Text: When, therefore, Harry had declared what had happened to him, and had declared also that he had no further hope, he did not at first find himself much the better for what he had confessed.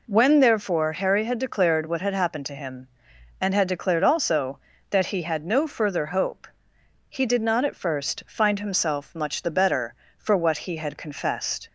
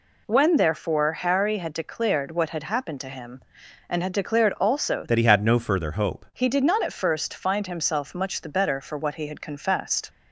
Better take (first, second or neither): first